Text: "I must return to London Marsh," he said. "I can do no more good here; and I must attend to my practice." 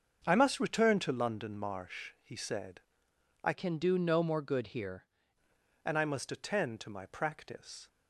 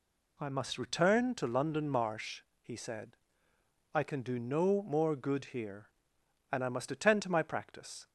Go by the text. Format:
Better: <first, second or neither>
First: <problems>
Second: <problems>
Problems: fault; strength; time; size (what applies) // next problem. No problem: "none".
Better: second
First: starts louder than the rest; until 1.2 s; 7 dB // changes voice from "can" to "here"; from 3.5 to 5.0 s; 1.5 s long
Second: none